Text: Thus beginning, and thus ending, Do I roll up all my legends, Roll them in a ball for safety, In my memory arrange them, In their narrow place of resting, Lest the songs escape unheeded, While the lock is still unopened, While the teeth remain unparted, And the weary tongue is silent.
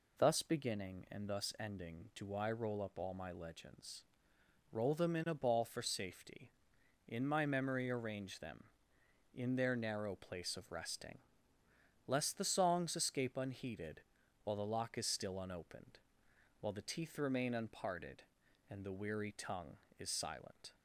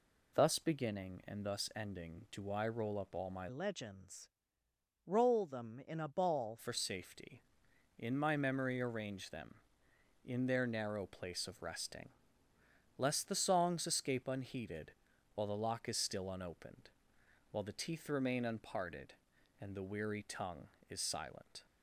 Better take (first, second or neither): first